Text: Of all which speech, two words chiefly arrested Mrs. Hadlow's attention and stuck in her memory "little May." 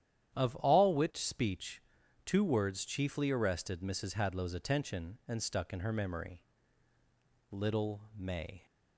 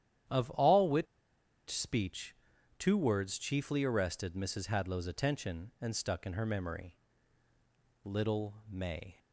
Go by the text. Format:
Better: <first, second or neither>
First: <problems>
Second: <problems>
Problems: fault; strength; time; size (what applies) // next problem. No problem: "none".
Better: first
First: starts louder than the rest; strong; until 1.4 s; 10 dB // pauses between "memory" and "little"; at 6.4 s; 1.1 s long // pauses between "little" and "May"; slight; at 8.0 s; 0.16 s long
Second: starts louder than the rest; strong; until 1.9 s; 10 dB // pauses between "which" and "speech"; noticeable; at 1.0 s; 0.64 s long // pauses between "memory" and "little"; at 6.9 s; 1.1 s long // pauses between "little" and "May"; slight; at 8.5 s; 0.16 s long